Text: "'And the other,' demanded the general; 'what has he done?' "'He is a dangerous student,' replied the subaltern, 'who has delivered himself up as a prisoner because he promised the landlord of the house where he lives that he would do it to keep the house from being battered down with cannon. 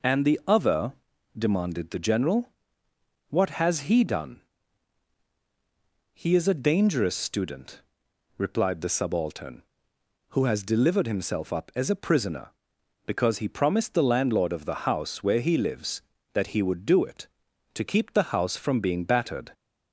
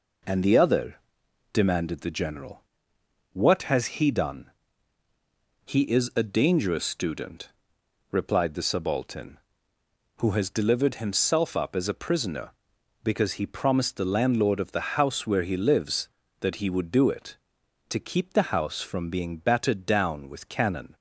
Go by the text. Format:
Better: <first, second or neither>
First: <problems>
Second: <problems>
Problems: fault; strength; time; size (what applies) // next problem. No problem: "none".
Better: second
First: stops before "down with cannon"; at 19.5 s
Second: none